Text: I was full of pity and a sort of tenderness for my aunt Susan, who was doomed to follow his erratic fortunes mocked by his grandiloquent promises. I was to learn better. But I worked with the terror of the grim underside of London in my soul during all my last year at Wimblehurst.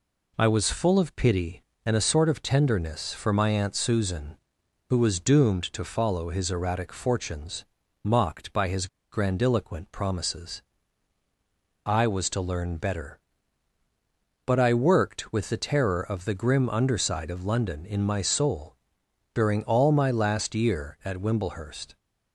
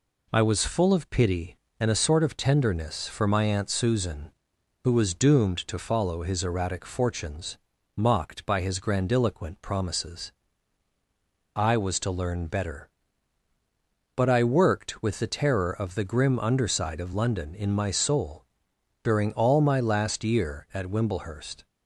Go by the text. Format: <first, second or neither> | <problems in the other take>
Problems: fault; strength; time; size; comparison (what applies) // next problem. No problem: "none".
second | pauses between "fortunes" and "mocked"; at 7.6 s; 0.38 s long; also in the second // pauses between "his" and "grandiloquent"; slight; at 8.8 s; 0.24 s long // pauses between "soul" and "during"; noticeable; at 18.7 s; 0.60 s long; noticeable in the second